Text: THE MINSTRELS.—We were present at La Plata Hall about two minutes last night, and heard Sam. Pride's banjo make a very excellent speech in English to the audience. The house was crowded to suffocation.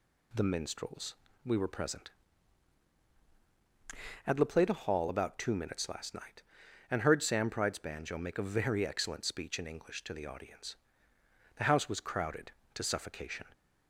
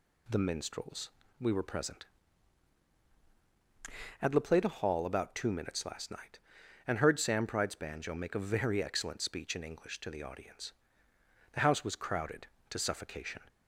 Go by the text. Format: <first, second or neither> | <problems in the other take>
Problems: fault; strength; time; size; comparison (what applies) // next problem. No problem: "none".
neither | none